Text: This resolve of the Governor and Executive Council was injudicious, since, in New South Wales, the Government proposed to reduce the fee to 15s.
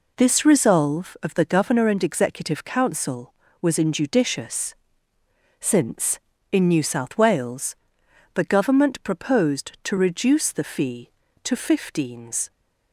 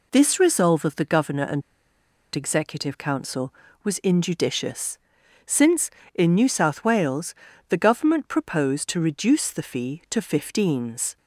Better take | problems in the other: first | pauses between "and" and "Executive"; noticeable; at 1.6 s; 0.72 s long

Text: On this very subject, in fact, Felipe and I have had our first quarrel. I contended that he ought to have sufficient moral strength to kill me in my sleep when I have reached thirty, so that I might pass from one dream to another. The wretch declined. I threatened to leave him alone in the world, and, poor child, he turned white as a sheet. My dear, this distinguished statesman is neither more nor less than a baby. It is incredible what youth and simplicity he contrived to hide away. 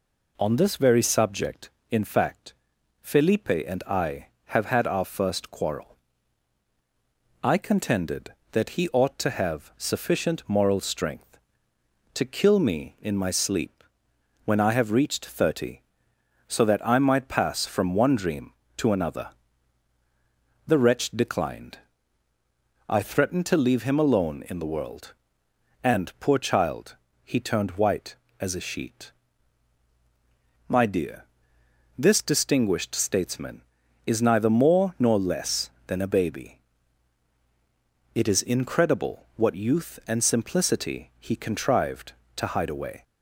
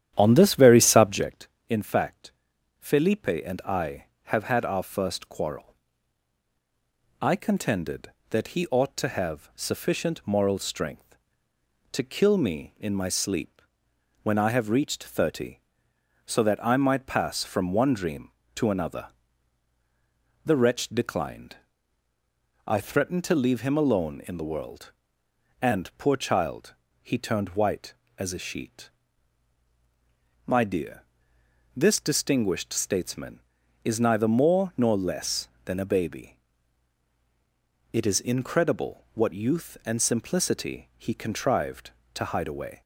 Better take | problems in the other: first | starts louder than the rest; strong; until 1.3 s; 10.5 dB // pauses between "sleep" and "when"; noticeable; at 13.5 s; 0.62 s long; noticeable in the first

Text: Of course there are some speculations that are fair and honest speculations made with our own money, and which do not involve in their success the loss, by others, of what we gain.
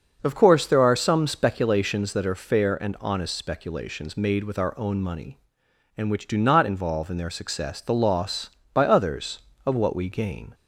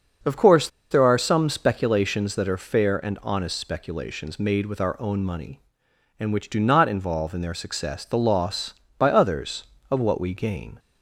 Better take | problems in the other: first | starts louder than the rest; until 1.4 s; 6 dB; also in the first // pauses between "course" and "there"; slight; at 0.6 s; 0.22 s long

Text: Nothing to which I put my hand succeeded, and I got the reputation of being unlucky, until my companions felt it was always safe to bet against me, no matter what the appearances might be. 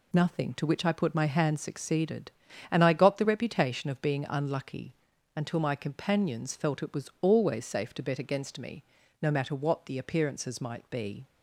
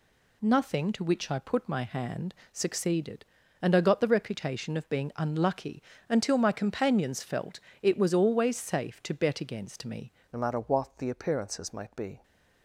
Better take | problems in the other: first | pauses between "hand" and "succeeded"; slight; at 2.3 s; 0.20 s long // pauses between "felt" and "it"; slight; at 7.5 s; 0.22 s long // changes voice at "no"; from 10.3 s on; 1.9 s long

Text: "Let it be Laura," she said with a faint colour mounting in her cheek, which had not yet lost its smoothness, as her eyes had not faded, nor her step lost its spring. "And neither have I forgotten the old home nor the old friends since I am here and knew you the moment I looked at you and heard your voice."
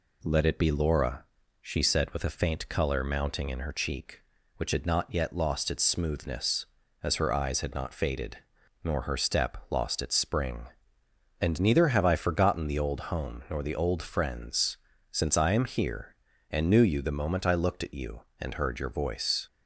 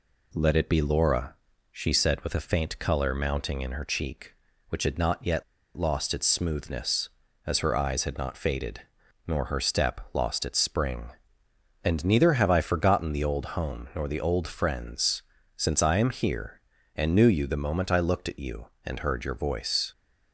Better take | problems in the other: first | pauses between "yet" and "lost"; slight; at 5.4 s; 0.34 s long // pauses between "friends" and "since"; slight; at 15.2 s; 0.32 s long; slight in the first

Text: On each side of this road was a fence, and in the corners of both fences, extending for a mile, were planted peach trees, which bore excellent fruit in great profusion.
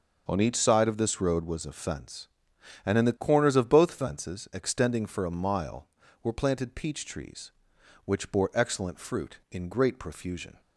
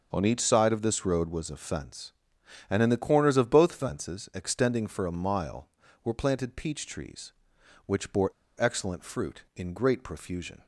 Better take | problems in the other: first | starts louder than the rest; noticeable; until 1.1 s; 6 dB; noticeable in the first // pauses between "bore" and "excellent"; slight; at 8.2 s; 0.29 s long

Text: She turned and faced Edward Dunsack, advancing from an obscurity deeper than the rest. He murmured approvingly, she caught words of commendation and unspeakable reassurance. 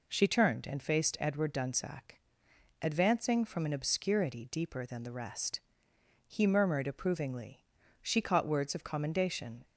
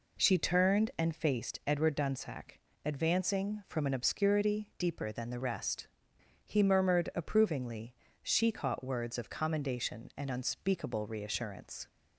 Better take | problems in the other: second | stops before "and unspeakable reassurance"; at 9.6 s

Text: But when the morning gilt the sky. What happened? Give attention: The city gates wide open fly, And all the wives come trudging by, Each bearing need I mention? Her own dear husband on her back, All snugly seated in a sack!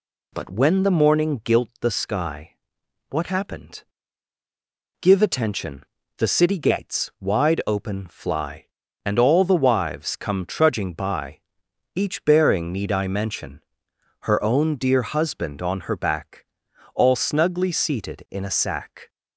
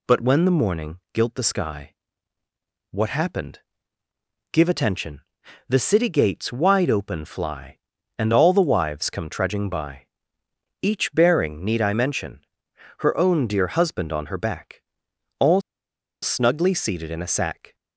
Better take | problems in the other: first | pauses between "morning" and "gilt"; slight; at 0.9 s; 0.16 s long // pauses between "All" and "snugly"; noticeable; at 15.6 s; 0.61 s long

